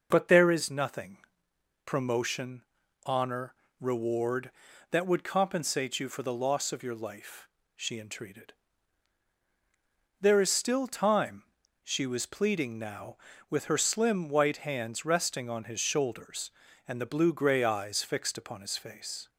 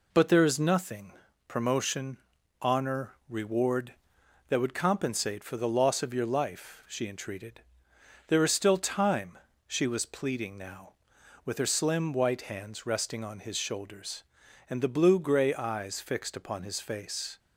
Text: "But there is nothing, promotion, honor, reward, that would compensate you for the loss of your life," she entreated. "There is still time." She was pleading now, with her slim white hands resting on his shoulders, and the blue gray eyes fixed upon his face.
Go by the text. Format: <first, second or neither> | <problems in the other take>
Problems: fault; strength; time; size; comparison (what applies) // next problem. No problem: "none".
first | skips "you"; at 5.4 s